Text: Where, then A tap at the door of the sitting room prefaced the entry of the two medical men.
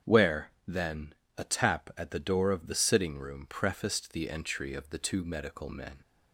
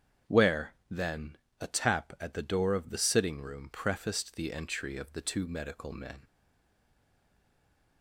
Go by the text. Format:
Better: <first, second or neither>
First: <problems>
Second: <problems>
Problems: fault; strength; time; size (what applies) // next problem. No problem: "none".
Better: first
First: starts louder than the rest; strong; until 1.4 s; 8 dB // pauses between "then" and "A"; slight; at 1.1 s; 0.24 s long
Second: starts louder than the rest; strong; until 1.7 s; 8 dB // pauses between "then" and "A"; slight; at 1.3 s; 0.24 s long // stays silent after the last word; noticeable; from 6.2 s on; 1.8 s long